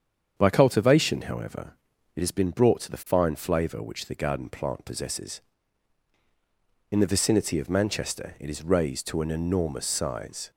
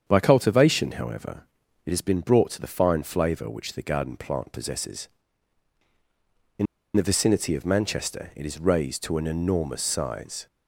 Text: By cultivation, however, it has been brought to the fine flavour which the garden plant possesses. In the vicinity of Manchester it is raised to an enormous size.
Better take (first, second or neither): first